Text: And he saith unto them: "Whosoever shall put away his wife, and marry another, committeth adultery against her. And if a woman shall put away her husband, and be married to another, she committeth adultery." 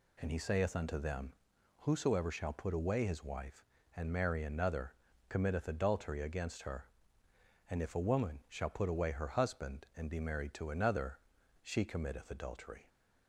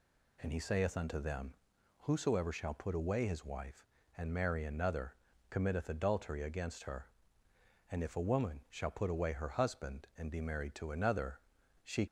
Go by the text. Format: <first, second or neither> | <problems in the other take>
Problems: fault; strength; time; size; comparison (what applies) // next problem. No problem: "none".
first | stops before "committeth adultery"; at 12.0 s